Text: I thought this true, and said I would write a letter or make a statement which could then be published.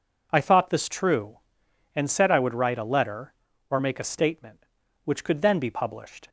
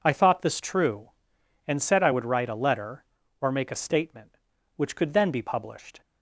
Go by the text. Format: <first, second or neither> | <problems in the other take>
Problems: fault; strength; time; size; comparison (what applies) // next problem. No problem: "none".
neither | none